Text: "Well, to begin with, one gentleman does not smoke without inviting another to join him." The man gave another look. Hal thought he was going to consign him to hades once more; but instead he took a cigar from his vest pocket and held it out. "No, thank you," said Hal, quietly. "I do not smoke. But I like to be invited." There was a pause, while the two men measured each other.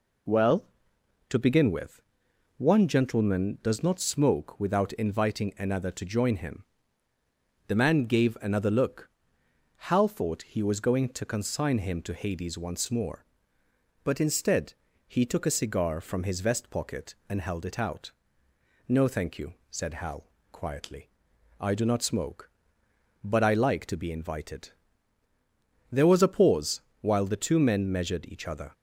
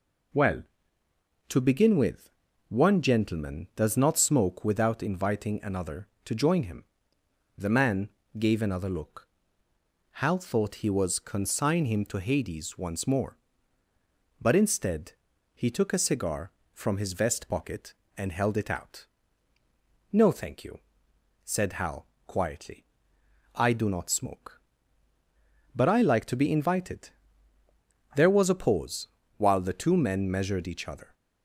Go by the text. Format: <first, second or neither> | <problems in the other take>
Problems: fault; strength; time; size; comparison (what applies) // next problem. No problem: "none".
first | pauses between "man" and "gave"; slight; at 8.0 s; 0.28 s long // skips "going to"; at 11.1 s // pauses between "instead" and "he"; at 15.1 s; 0.42 s long; slight in the first